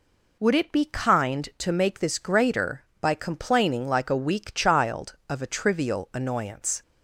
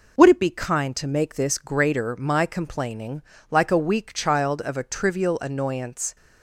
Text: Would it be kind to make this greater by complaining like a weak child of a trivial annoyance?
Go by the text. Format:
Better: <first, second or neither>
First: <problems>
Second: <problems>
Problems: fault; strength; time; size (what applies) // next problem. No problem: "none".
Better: first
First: none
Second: says "my" for "by"; at 2.1 s // pauses between "complaining" and "like"; slight; at 3.2 s; 0.28 s long